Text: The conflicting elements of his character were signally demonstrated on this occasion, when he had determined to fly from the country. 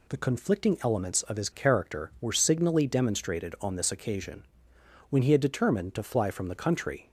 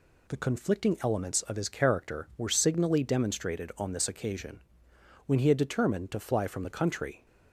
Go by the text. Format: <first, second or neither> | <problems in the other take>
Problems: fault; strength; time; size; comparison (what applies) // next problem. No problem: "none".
neither | none